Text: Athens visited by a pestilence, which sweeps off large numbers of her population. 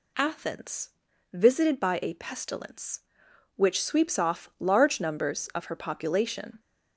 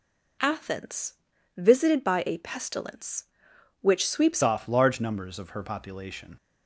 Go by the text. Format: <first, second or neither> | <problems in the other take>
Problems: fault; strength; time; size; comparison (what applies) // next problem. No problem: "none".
first | pauses between "Athens" and "visited"; at 1.1 s; 0.42 s long; also in the first // changes voice at "off"; from 4.4 s on; 1.9 s long